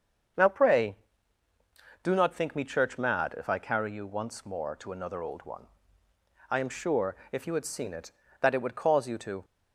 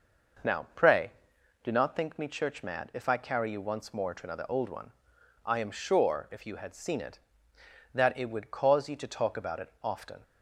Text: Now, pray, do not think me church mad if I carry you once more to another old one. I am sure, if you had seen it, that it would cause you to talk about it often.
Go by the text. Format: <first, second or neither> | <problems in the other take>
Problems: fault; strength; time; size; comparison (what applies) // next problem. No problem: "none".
second | starts louder than the rest; until 2.4 s; 7 dB // stops before "talk about it often"; at 9.4 s